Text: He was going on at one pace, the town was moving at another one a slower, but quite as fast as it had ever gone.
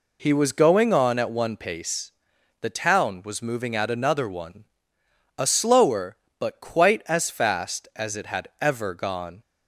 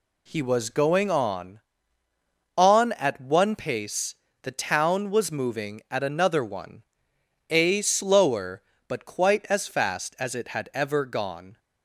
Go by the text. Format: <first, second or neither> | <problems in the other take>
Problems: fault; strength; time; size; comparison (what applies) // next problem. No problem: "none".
first | says "on" twice; at 2.5 s // pauses between "one" and "a"; noticeable; at 6.8 s; 0.66 s long; noticeable in the first